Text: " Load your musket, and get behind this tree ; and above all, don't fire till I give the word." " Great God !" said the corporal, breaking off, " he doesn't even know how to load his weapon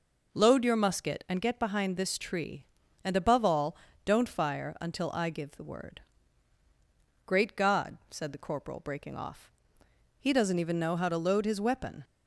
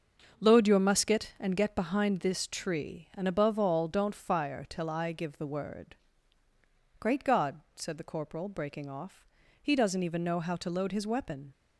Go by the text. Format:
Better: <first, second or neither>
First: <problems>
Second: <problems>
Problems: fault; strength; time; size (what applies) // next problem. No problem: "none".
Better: second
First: starts louder than the rest; noticeable; until 1.3 s; 6 dB // says "until" for "till"; at 4.7 s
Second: starts louder than the rest; until 1.2 s; 6.5 dB